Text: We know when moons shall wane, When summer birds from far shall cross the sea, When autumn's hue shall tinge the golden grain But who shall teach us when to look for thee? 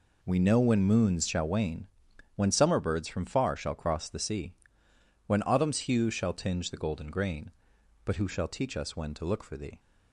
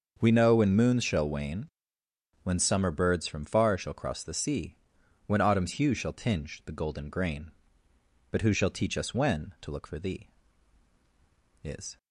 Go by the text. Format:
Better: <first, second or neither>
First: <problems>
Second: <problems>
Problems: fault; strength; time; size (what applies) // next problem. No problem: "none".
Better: first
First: none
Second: starts louder than the rest; until 1.2 s; 6 dB // goes on to say "Is"; slight; from 11.6 s on; 0.34 s long